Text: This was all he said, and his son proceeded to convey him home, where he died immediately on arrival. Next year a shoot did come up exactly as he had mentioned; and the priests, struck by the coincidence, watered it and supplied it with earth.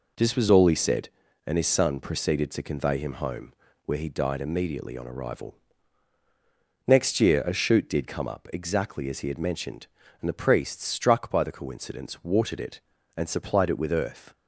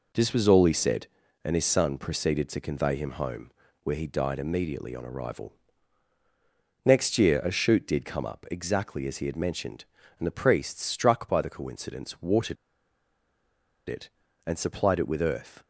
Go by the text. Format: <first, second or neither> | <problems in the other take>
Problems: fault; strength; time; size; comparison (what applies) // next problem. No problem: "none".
first | pauses between "watered" and "it"; strong; at 12.5 s; 1.3 s long